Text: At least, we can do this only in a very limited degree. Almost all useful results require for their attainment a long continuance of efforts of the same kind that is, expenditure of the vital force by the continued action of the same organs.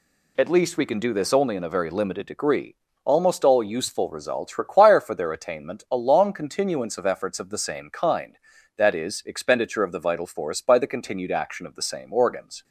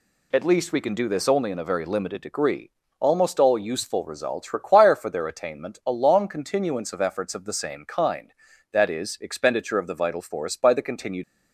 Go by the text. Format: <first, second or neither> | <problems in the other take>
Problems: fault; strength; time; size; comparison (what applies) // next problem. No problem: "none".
first | stops before "action of the same organs"; at 11.2 s